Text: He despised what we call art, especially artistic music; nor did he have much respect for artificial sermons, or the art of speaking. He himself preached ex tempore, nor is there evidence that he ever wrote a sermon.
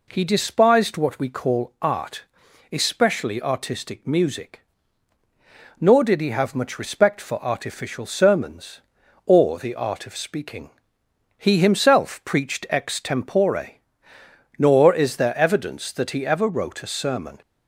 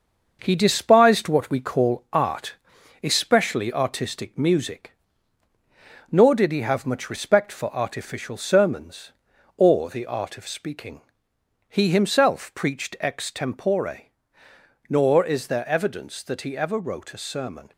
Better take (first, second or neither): first